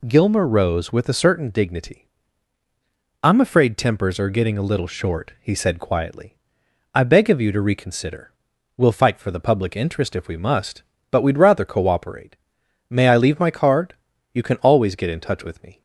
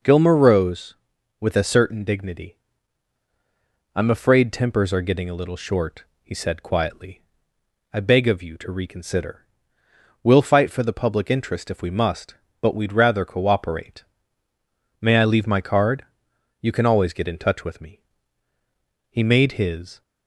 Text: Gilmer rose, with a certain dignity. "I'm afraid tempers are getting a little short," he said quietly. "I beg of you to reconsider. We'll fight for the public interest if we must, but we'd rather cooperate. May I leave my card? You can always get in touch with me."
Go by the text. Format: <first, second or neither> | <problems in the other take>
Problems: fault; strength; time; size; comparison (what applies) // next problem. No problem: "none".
first | goes on to say "He made his"; noticeable; from 19.0 s on; 0.94 s long